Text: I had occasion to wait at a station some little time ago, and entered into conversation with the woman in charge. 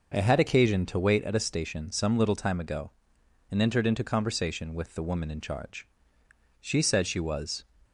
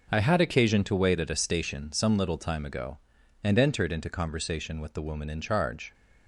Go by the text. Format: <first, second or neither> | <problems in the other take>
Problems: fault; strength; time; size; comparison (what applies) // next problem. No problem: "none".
second | goes on to say "She said she was"; noticeable; from 6.6 s on; 1.0 s long